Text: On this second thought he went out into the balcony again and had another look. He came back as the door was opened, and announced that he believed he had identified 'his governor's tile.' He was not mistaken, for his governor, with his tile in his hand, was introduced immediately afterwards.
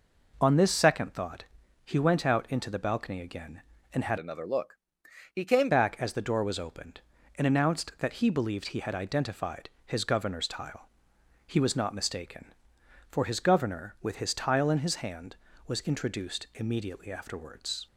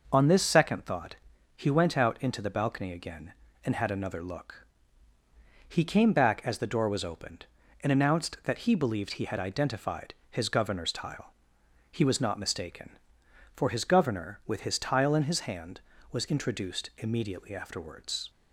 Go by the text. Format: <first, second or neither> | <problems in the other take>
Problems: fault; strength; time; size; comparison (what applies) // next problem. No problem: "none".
second | pauses between "thought" and "he"; at 1.4 s; 0.40 s long; also in the second // changes voice from "another" to "came"; from 4.1 to 5.6 s; 1.5 s long // pauses between "identified" and "his"; slight; at 9.6 s; 0.16 s long; slight in the second